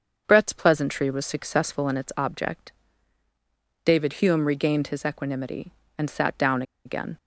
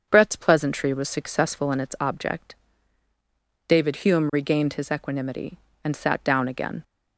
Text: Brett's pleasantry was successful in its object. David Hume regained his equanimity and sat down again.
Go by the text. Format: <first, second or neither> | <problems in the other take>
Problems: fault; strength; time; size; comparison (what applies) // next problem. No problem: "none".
second | starts louder than the rest; until 1.3 s; 6.5 dB; also in the second // pauses between "down" and "again"; slight; at 6.6 s; 0.22 s long